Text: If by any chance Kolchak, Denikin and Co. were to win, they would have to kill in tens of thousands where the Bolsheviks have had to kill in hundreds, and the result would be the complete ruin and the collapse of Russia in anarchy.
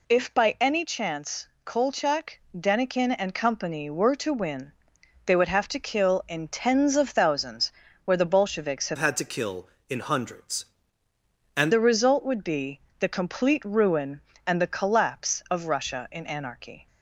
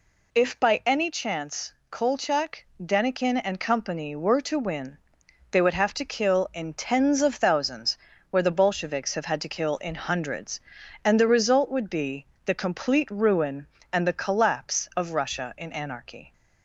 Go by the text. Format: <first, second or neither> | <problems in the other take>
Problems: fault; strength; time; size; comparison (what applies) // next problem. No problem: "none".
second | pauses between "chance" and "Kolchak"; slight; at 1.4 s; 0.18 s long; slight in the second // pauses between "thousands" and "where"; slight; at 7.7 s; 0.32 s long; slight in the second // changes voice from "had" to "and"; from 8.9 to 11.7 s; 2.8 s long // pauses between "be" and "the"; slight; at 12.7 s; 0.20 s long; slight in the second